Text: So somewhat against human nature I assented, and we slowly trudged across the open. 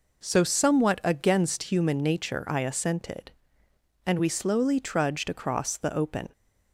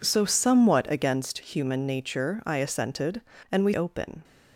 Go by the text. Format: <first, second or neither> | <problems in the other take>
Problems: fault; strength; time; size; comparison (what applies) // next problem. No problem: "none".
first | skips "slowly trudged across the"; at 3.7 s